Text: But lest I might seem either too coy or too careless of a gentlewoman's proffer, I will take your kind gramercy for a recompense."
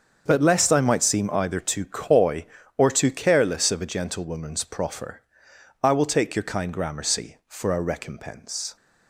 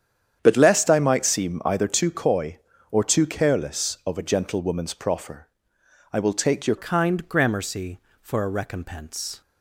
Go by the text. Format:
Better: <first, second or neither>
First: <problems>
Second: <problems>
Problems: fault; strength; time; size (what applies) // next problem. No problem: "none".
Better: first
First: starts louder than the rest; until 1.2 s; 7 dB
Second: starts louder than the rest; strong; until 1.4 s; 8.5 dB // changes voice at "kind"; from 6.7 s on; 2.7 s long